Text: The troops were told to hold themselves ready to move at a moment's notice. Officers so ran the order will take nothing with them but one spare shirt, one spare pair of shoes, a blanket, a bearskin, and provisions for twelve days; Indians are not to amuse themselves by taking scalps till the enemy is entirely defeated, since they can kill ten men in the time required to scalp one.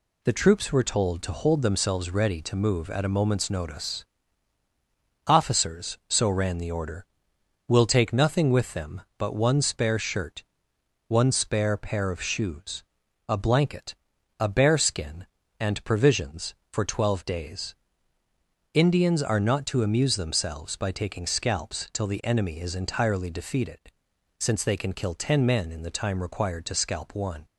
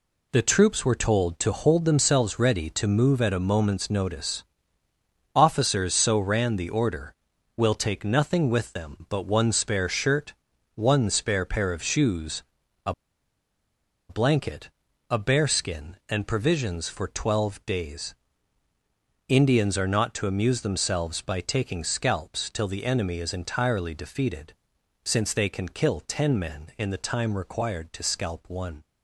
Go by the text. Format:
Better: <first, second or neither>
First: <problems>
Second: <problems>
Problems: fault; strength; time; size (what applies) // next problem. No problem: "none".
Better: first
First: none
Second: pauses between "a" and "blanket"; at 12.9 s; 1.1 s long